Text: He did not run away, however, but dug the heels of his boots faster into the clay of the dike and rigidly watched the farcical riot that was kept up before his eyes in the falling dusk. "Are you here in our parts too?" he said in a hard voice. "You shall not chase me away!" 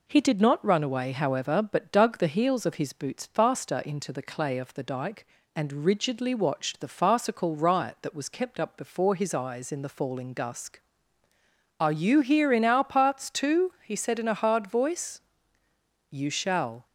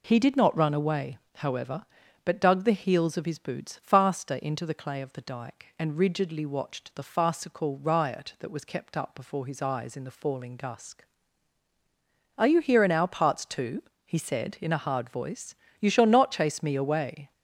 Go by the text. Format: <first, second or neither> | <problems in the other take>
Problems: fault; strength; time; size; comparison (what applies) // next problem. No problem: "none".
second | stops before "not chase me away"; at 16.8 s